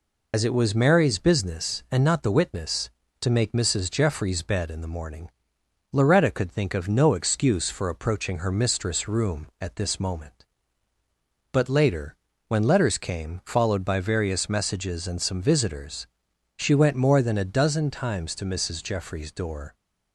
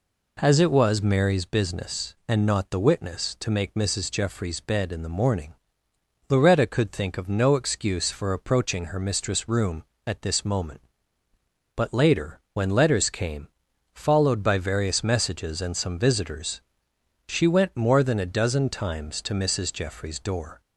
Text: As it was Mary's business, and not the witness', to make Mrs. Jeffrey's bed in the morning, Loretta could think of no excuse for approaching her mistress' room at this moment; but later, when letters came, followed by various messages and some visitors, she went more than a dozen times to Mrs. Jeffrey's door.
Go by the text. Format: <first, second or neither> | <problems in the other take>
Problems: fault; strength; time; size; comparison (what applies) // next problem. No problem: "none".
second | loses the start of "As"; at 0.3 s; 60 ms